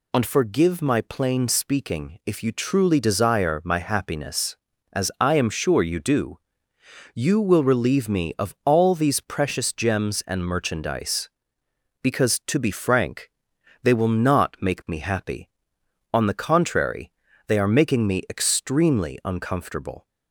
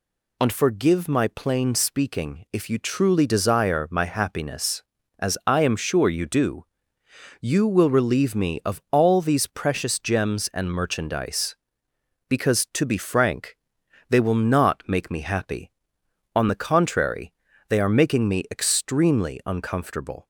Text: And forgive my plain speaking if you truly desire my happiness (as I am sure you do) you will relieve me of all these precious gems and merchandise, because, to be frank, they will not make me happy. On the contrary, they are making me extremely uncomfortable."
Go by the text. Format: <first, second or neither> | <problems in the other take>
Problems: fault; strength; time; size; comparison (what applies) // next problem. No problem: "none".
neither | none